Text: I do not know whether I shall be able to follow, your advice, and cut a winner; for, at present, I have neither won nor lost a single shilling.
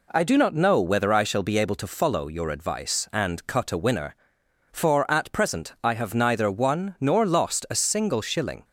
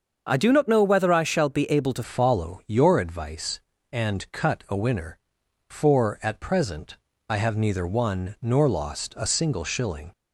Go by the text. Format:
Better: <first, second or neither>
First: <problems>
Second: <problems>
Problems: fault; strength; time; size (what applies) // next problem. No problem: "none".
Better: first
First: none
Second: starts louder than the rest; until 1.3 s; 6.5 dB // changes voice at "follow"; from 2.0 s on; 8.1 s long